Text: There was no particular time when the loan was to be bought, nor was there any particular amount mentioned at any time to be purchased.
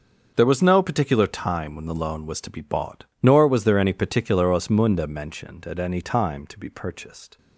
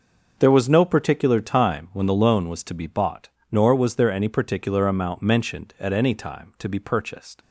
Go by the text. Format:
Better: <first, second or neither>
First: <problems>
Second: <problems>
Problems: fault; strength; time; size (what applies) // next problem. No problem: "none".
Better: second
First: starts louder than the rest; until 1.3 s; 6.5 dB // says "osmunda" for "amount"; at 4.4 s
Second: starts louder than the rest; until 1.3 s; 6 dB